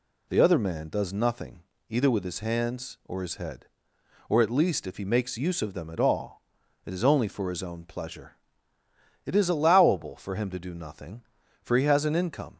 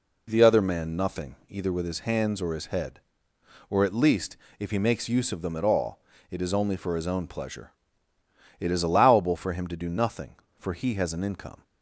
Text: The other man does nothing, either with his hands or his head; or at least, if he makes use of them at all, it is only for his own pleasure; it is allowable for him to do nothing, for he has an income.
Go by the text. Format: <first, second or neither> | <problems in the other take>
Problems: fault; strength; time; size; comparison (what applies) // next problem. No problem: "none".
first | skips "does"; at 0.9 s